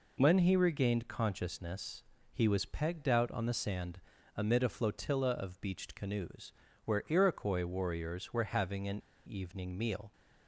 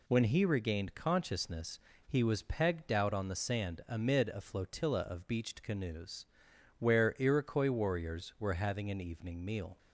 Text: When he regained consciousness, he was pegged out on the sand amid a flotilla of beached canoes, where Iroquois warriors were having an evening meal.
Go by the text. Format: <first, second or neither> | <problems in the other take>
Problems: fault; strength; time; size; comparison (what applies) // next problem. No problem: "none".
second | pauses between "sand" and "amid"; slight; at 4.0 s; 0.34 s long // pauses between "an" and "evening"; slight; at 8.9 s; 0.27 s long